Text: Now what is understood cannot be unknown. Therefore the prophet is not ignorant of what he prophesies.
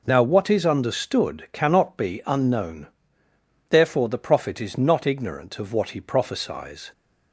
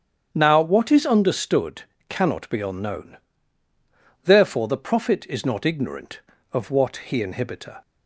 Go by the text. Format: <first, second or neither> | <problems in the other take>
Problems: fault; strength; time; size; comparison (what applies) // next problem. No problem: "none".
first | starts louder than the rest; strong; until 1.3 s; 8.5 dB // pauses between "understood" and "cannot"; slight; at 1.8 s; 0.26 s long // says "inhibitor" for "prophesies"; at 7.2 s